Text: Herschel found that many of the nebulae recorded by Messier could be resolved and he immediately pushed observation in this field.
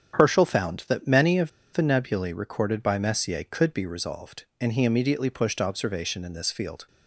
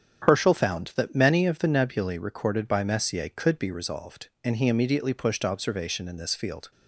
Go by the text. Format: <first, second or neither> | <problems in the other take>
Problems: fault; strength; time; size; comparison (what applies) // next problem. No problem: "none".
second | starts louder than the rest; strong; until 1.2 s; 8.5 dB; strong in the second // pauses between "of" and "the"; slight; at 1.5 s; 0.22 s long